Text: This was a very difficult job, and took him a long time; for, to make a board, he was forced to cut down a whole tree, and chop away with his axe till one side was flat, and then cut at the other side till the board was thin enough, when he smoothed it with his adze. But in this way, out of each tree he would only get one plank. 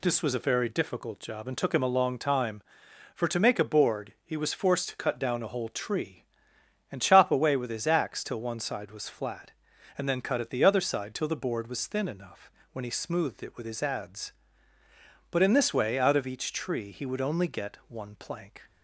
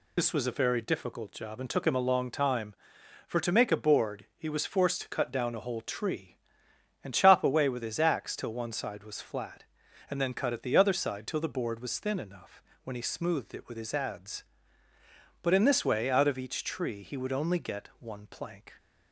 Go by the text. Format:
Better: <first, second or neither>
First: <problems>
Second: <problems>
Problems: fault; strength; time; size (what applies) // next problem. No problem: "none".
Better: first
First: none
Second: loses the start of "This"; at 0.1 s; 55 ms